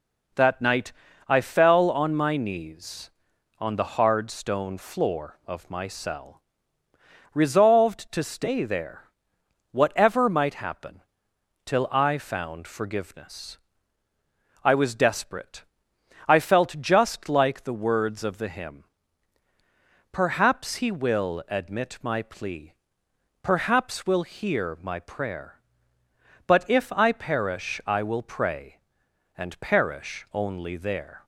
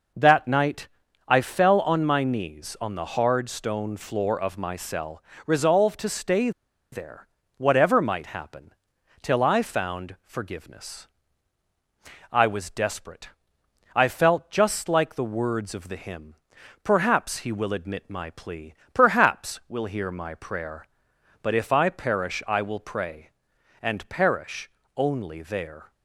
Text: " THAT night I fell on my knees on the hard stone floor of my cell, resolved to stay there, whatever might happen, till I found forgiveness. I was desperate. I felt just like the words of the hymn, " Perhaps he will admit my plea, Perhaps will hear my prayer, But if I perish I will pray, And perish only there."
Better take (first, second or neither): first